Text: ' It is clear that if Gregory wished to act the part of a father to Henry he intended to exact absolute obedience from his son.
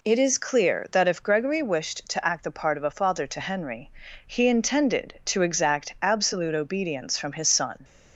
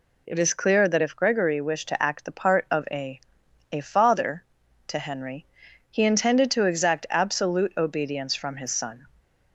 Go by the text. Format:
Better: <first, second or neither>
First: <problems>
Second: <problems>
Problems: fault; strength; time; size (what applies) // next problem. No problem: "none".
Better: first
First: pauses between "Henry" and "he"; at 3.9 s; 0.38 s long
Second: says "a" twice; at 3.7 s // pauses between "Henry" and "he"; noticeable; at 5.4 s; 0.46 s long